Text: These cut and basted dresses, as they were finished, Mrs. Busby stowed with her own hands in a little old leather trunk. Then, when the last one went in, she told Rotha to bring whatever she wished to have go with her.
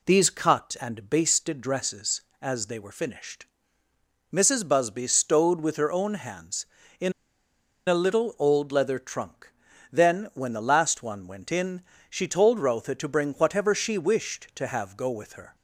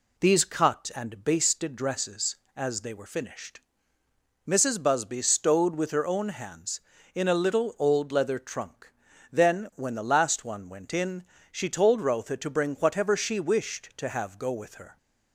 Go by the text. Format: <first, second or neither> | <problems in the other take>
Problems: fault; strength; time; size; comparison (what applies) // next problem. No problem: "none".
second | pauses between "in" and "a"; noticeable; at 7.1 s; 0.74 s long